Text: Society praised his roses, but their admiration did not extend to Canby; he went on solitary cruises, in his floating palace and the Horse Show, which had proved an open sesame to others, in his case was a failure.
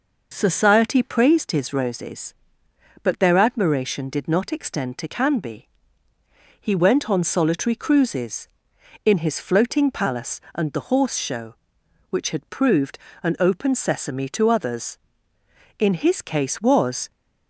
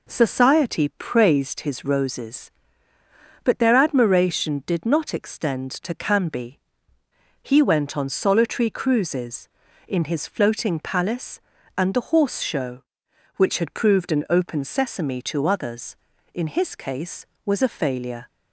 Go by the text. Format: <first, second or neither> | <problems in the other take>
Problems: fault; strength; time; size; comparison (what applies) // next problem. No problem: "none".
second | pauses between "proved" and "an"; slight; at 12.9 s; 0.26 s long // stops before "a failure"; at 17.1 s